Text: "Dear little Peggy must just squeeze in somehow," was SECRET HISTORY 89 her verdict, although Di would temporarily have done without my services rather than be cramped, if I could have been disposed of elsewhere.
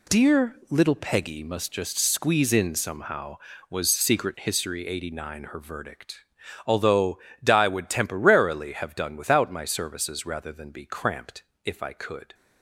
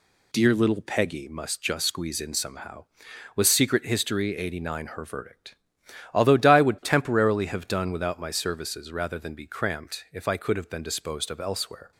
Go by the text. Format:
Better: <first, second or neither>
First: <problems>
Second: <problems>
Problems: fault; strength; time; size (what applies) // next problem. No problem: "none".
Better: second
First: pauses between "although" and "Di"; slight; at 7.1 s; 0.24 s long // stops before "have been disposed of elsewhere"; at 12.3 s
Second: none